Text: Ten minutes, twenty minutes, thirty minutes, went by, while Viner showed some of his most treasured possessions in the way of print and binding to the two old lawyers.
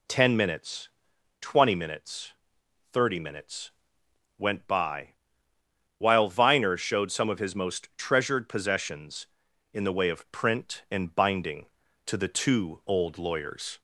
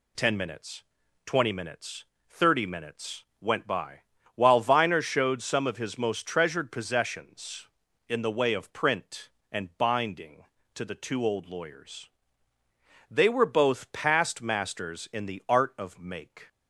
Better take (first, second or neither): first